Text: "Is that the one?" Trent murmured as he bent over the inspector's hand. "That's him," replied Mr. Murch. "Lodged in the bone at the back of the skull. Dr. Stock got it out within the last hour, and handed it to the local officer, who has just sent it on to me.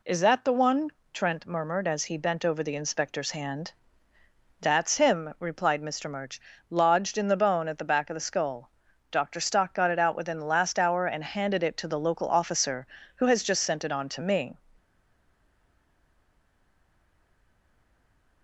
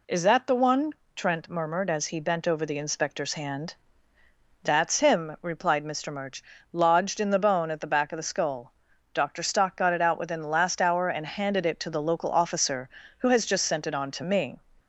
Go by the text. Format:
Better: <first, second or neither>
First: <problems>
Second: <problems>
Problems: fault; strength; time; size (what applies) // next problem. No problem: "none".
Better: second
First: stays silent after the last word; strong; from 14.7 s on; 3.7 s long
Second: none